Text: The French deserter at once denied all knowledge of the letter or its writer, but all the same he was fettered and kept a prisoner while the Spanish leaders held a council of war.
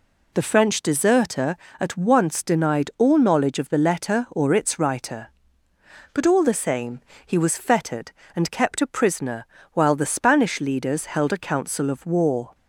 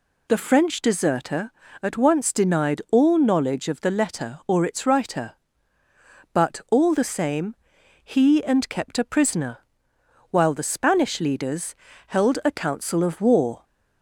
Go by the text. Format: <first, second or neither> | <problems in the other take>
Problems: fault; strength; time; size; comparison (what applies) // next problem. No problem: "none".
first | pauses between "same" and "he"; noticeable; at 7.5 s; 0.46 s long; slight in the first // skips "was fettered"; at 8.4 s // pauses between "prisoner" and "while"; noticeable; at 9.5 s; 0.72 s long; slight in the first // pauses between "leaders" and "held"; slight; at 11.7 s; 0.32 s long